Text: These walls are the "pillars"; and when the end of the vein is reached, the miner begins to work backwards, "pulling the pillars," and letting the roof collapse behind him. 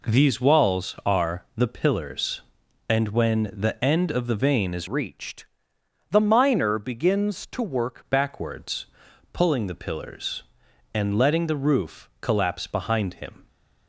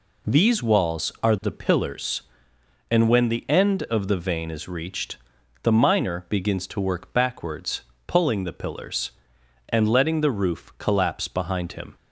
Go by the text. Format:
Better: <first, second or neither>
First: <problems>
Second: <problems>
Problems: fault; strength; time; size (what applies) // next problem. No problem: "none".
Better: second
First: changes voice from "reached" to "work"; from 4.8 to 8.0 s; 3.2 s long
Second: none